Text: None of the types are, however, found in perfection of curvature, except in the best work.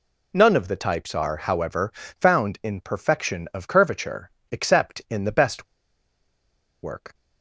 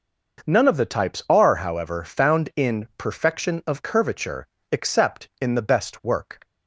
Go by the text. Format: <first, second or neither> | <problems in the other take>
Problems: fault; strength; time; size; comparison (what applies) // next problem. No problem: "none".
second | pauses between "best" and "work"; at 5.6 s; 1.1 s long